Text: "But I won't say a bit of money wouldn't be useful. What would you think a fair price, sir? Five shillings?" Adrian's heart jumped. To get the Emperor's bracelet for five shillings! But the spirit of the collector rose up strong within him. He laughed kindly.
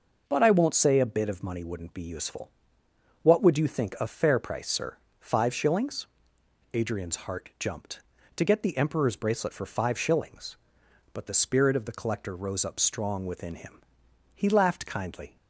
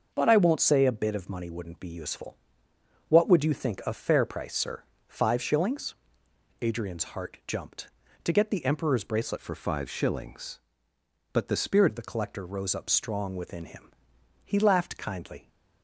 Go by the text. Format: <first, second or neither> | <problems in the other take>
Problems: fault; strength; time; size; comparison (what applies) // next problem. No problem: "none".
first | starts louder than the rest; noticeable; until 1.1 s; 6 dB // changes voice from "for" to "spirit"; from 9.3 to 11.9 s; 2.6 s long